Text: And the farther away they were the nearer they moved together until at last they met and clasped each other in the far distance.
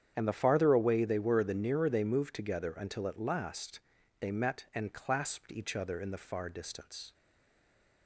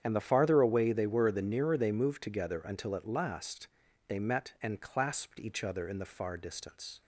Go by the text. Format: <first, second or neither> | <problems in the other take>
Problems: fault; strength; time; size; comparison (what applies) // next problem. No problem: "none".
second | starts louder than the rest; strong; until 1.1 s; 8.5 dB; strong in the second // pauses between "last" and "they"; at 3.7 s; 0.40 s long; also in the second // stays silent after the last word; slight; from 7.1 s on; 0.9 s long